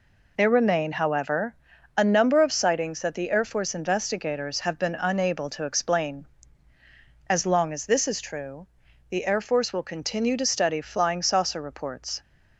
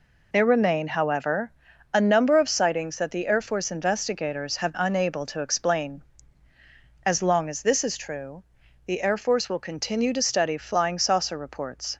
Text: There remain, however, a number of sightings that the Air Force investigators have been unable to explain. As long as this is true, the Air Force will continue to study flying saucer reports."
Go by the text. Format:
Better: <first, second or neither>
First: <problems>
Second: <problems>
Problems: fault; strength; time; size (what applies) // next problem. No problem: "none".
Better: first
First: none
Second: skips "been"; at 4.7 s